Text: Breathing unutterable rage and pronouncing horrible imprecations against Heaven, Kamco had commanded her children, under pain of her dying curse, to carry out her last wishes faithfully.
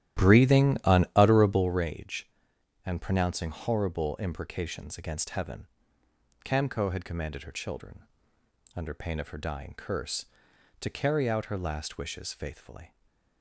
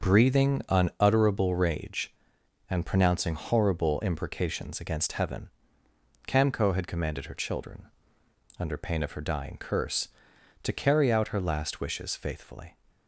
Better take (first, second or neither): second